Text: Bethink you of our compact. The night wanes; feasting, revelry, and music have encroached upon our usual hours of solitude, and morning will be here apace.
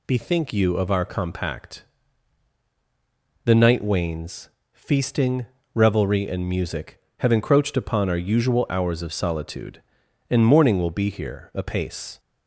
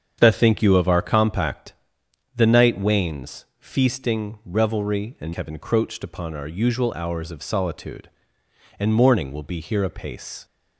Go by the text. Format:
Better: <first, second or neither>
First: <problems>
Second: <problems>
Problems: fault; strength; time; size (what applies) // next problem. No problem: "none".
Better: first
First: none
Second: starts louder than the rest; strong; until 1.2 s; 8 dB // skips "music"; at 5.3 s